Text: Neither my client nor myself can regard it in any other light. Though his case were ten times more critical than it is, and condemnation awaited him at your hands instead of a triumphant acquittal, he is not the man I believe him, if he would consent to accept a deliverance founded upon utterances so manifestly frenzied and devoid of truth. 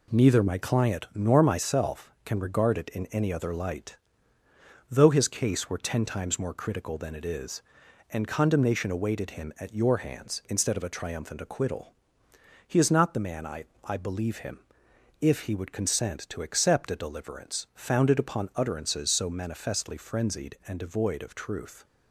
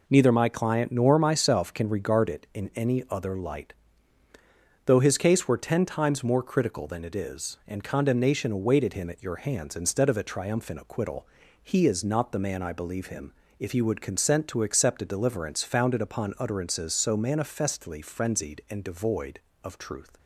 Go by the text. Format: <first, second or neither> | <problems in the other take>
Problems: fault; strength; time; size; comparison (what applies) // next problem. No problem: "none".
second | says "I" twice; at 13.8 s